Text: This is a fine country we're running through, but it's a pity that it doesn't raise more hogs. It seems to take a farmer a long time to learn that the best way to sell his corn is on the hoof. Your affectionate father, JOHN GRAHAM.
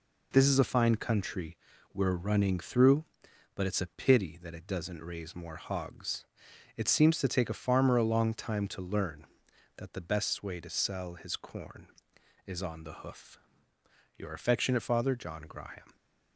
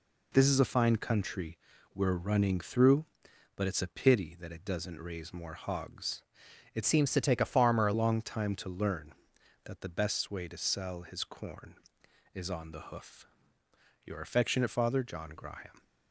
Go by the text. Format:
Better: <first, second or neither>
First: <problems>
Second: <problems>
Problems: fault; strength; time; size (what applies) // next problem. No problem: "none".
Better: first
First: pauses between "country" and "we're"; slight; at 1.5 s; 0.34 s long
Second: pauses between "country" and "we're"; slight; at 1.5 s; 0.34 s long // changes voice from "seems" to "a"; from 6.8 to 7.9 s; 1.1 s long